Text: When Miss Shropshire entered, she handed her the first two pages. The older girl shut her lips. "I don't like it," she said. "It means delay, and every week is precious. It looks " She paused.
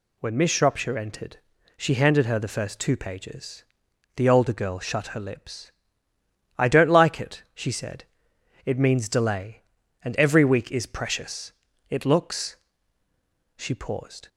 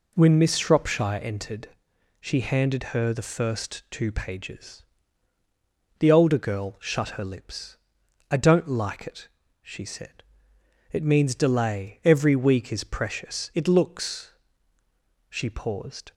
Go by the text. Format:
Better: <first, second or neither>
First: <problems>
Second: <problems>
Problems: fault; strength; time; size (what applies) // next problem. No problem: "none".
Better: first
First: none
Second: skips "and"; at 12.0 s